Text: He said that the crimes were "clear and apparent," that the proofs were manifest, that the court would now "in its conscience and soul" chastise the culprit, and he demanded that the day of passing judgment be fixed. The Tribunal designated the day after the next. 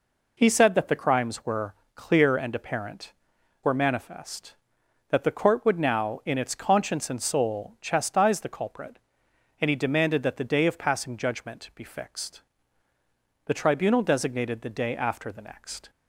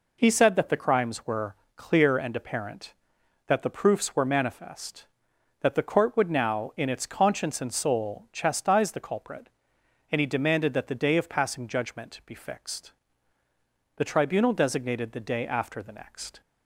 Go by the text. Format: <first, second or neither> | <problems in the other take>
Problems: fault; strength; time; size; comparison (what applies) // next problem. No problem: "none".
second | pauses between "were" and "clear"; slight; at 1.7 s; 0.22 s long; slight in the second // skips "that the proofs"; at 3.3 s